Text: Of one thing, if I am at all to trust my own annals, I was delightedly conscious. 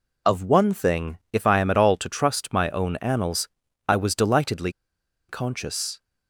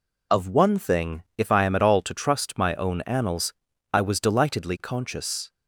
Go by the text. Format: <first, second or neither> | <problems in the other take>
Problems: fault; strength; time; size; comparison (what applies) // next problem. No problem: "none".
second | pauses between "delightedly" and "conscious"; noticeable; at 4.6 s; 0.58 s long